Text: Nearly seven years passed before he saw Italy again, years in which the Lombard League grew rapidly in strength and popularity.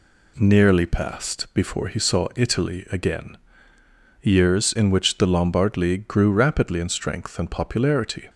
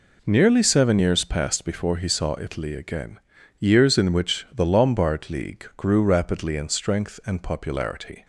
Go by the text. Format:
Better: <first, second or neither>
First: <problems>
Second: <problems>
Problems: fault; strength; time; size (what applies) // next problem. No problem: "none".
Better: second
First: skips "seven years"; at 0.8 s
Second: none